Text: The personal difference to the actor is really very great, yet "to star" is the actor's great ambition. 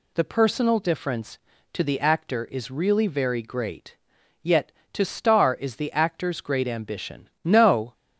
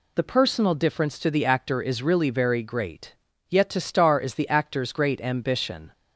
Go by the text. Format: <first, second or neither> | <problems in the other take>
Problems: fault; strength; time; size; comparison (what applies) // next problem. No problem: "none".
second | goes on to say "No"; slight; from 7.4 s on; 0.48 s long